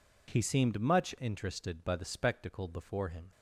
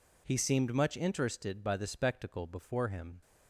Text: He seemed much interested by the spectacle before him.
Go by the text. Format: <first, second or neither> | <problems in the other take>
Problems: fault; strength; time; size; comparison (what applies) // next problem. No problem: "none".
neither | none